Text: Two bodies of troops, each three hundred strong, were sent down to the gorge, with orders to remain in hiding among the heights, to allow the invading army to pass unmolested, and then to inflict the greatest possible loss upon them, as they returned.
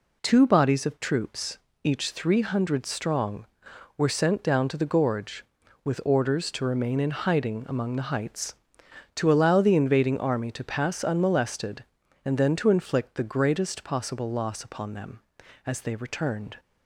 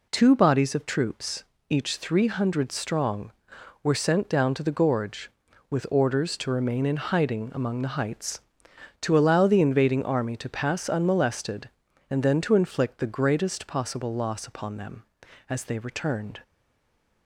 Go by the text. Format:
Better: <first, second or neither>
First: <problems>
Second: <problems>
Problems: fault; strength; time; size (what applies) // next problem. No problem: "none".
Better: first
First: none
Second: stays silent after the last word; slight; from 16.4 s on; 0.8 s long